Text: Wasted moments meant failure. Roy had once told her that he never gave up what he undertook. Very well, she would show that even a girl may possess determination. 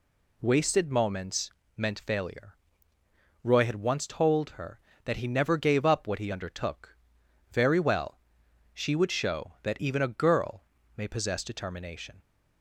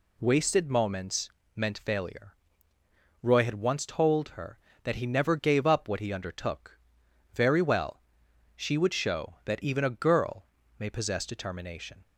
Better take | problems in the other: neither | pauses between "moments" and "meant"; slight; the same in both // pauses between "girl" and "may"; slight; the same in both

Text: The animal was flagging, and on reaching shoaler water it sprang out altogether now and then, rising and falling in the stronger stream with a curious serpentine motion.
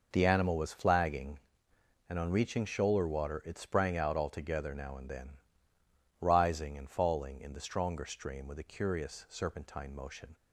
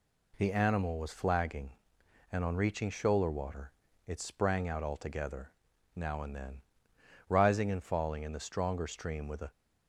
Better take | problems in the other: first | pauses between "water" and "it"; slight; at 3.7 s; 0.34 s long // pauses between "altogether" and "now"; at 5.5 s; 0.44 s long // stops before "curious serpentine motion"; at 9.5 s

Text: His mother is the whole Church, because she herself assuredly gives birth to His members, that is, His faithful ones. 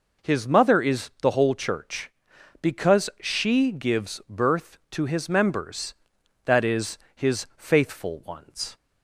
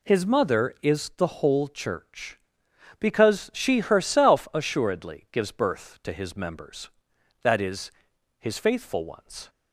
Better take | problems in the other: second | skips "herself assuredly"; at 3.7 s

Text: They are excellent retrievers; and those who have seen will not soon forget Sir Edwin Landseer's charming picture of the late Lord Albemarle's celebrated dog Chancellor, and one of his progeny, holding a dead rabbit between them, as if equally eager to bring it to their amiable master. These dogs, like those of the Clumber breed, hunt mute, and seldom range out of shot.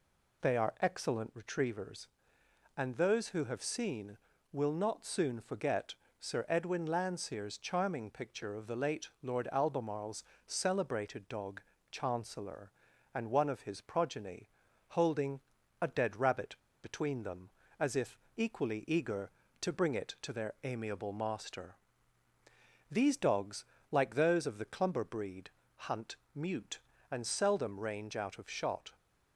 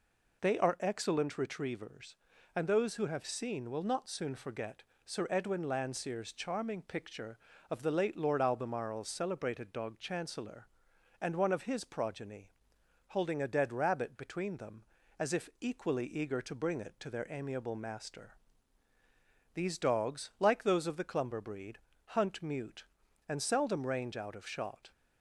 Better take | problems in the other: second | pauses between "forget" and "Sir"; slight; at 5.9 s; 0.24 s long; slight in the second // pauses between "Albemarle's" and "celebrated"; slight; at 10.2 s; 0.22 s long // pauses between "dog" and "Chancellor"; slight; at 11.5 s; 0.30 s long // pauses between "holding" and "a"; at 15.3 s; 0.42 s long // pauses between "rabbit" and "between"; slight; at 16.5 s; 0.26 s long // pauses between "if" and "equally"; slight; at 18.1 s; 0.20 s long // pauses between "hunt" and "mute"; slight; at 26.1 s; 0.20 s long

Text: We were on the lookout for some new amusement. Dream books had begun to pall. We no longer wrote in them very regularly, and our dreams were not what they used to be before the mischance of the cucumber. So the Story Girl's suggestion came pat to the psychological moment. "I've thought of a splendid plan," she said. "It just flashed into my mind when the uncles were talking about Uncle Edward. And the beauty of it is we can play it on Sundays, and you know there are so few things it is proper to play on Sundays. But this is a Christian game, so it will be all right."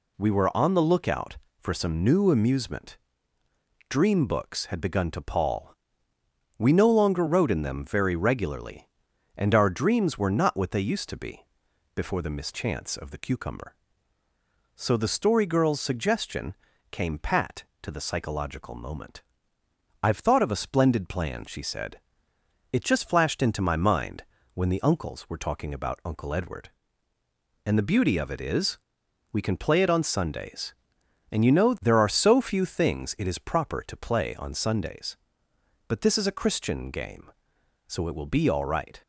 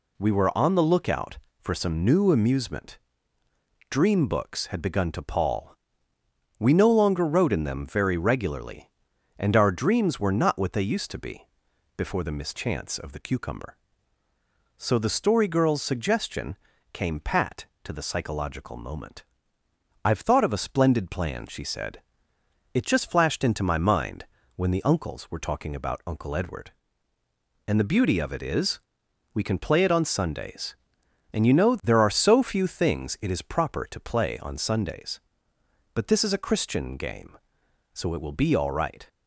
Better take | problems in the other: neither | pauses between "be" and "before"; noticeable; the same in both // pauses between "suggestion" and "came"; the same in both // pauses between "mind" and "when"; slight; the same in both // pauses between "is" and "we"; noticeable; the same in both

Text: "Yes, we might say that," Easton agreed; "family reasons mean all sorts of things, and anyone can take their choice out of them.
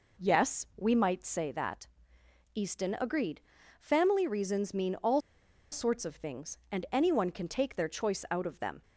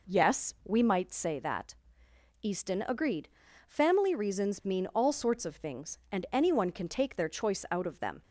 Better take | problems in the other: second | pauses between "all" and "sorts"; noticeable; at 5.2 s; 0.51 s long

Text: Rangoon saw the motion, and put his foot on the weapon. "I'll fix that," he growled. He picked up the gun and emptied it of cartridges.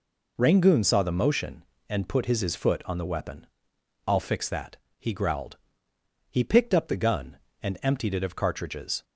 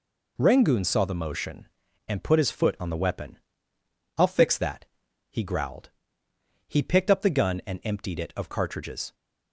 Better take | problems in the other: second | says "his" twice; at 2.3 s

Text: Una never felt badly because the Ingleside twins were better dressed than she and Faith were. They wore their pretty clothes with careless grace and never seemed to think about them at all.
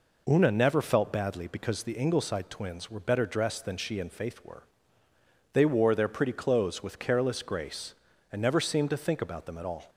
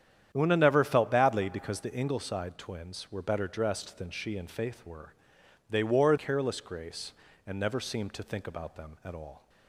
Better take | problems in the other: first | starts louder than the rest; strong; until 1.3 s; 9.5 dB // skips "their pretty clothes with"; at 6.1 s

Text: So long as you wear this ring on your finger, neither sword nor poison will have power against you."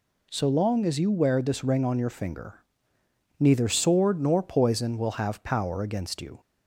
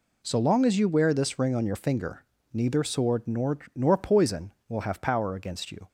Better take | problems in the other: first | says "nor" twice; at 3.7 s

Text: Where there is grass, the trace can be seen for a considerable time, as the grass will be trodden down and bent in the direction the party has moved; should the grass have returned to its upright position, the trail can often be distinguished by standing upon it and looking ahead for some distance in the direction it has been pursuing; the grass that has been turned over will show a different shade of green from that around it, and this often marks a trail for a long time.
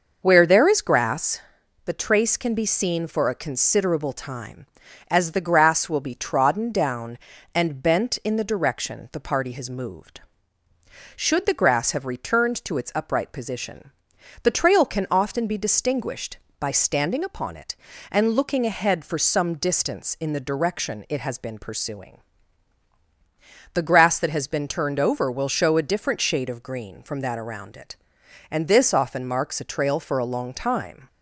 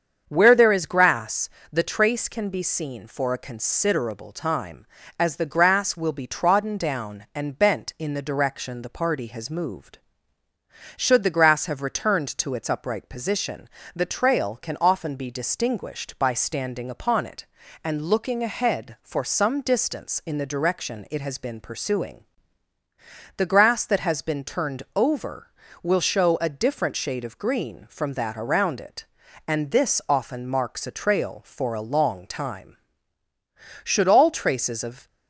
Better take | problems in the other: first | starts louder than the rest; strong; until 1.2 s; 7.5 dB // goes on to say "Should all traces of"; noticeable; from 33.8 s on; 1.2 s long

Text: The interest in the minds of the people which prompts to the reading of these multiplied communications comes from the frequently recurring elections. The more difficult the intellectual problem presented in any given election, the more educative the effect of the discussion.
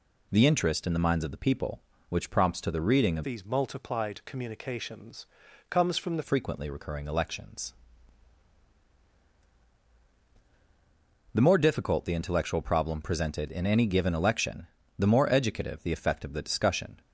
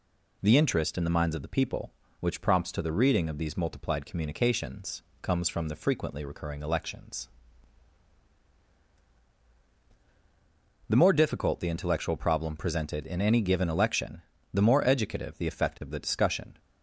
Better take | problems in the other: second | changes voice from "these" to "the"; from 3.2 to 6.2 s; 3.0 s long // pauses between "communications" and "comes"; at 5.2 s; 0.44 s long; slight in the second

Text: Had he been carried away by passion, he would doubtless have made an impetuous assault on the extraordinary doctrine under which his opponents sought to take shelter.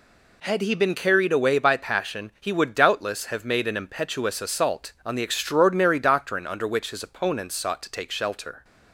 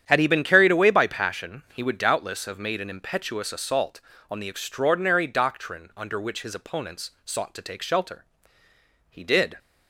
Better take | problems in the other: first | starts louder than the rest; strong; until 1.0 s; 9 dB // goes on to say "He did"; slight; from 9.0 s on; 0.48 s long

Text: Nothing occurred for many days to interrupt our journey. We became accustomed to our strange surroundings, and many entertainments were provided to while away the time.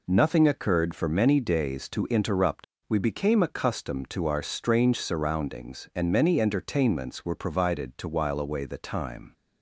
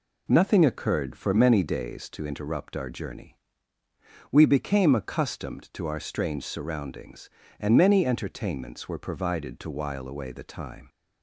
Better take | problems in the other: second | skips "our journey"; at 2.7 s

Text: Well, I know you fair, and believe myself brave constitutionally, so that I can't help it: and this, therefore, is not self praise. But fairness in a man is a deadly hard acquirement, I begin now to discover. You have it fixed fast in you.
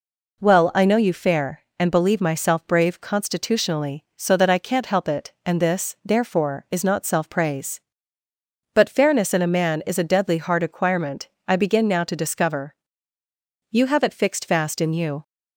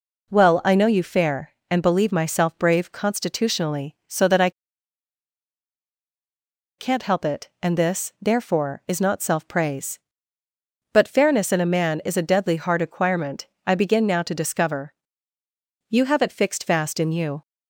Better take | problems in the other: first | pauses between "I" and "can't"; strong; at 4.4 s; 2.2 s long

